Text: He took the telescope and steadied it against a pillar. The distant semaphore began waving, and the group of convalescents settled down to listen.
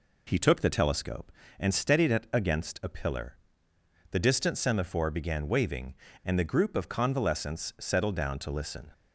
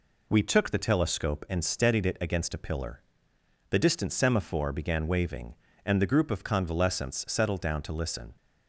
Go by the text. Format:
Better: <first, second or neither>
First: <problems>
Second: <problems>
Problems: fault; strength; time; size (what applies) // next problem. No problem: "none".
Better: first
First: none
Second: says "We" for "He"; at 0.3 s